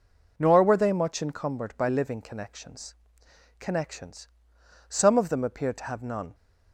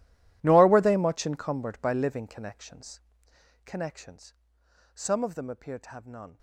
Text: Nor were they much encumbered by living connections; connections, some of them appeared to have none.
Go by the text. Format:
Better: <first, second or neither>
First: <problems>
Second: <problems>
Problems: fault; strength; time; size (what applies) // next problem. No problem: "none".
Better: first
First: none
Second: gets quieter; strong; throughout; 19.5 dB